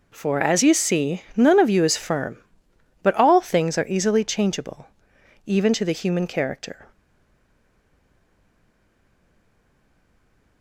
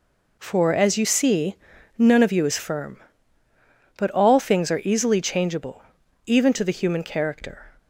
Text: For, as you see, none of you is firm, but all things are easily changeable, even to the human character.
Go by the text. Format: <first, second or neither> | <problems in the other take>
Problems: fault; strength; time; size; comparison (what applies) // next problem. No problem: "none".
second | stays silent after the last word; strong; from 6.9 s on; 3.7 s long